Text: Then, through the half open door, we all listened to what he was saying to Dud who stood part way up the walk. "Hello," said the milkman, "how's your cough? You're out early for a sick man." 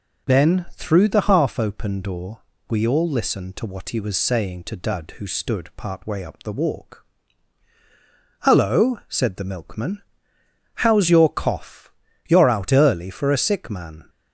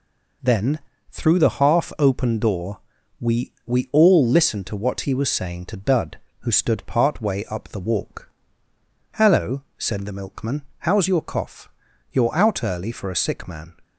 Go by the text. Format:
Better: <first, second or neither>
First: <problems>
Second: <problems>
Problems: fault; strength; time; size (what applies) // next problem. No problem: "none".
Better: first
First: none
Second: says "we" twice; at 3.6 s